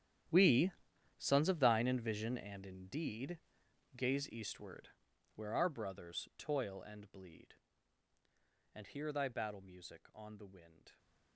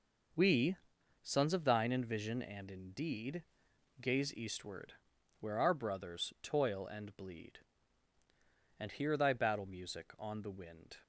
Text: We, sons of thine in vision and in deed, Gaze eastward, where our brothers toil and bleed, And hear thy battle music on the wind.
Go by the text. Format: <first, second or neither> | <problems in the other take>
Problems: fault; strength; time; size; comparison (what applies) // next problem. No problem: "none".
second | gets quieter; strong; throughout; 18 dB